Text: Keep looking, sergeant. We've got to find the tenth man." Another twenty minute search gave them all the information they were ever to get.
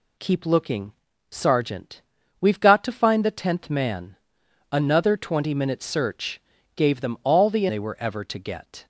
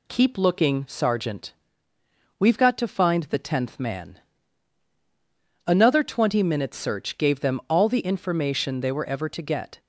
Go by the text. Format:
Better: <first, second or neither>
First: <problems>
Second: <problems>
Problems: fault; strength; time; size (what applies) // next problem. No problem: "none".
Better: second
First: pauses between "search" and "gave"; slight; at 6.4 s; 0.34 s long // skips "information"; at 7.6 s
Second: none